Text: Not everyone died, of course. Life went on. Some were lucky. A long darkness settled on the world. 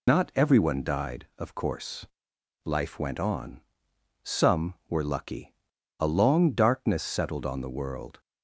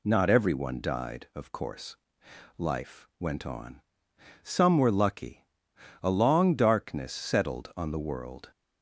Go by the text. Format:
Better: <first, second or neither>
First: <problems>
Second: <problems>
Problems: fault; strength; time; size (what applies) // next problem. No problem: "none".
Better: second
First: loses the start of "Not"; at 0.0 s; 70 ms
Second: none